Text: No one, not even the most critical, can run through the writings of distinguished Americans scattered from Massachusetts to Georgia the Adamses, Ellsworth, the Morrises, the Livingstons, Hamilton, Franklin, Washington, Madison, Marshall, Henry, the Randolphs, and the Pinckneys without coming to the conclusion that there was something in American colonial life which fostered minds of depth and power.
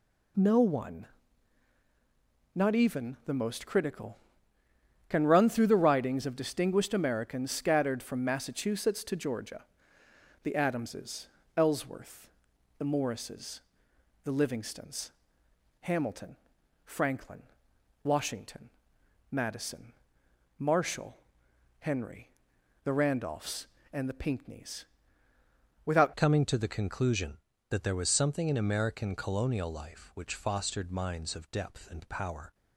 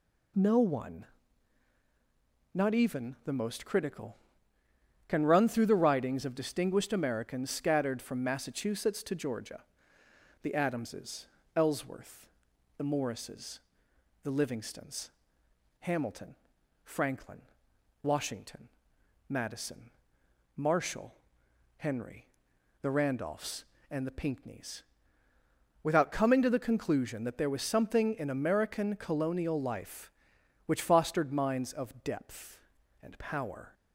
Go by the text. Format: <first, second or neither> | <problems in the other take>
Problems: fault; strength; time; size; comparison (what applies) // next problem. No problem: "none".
second | pauses between "Georgia" and "the"; noticeable; at 9.6 s; 0.80 s long; noticeable in the second // pauses between "Pinckneys" and "without"; at 24.8 s; 1.0 s long; also in the second // changes voice at "coming"; from 26.1 s on; 6.4 s long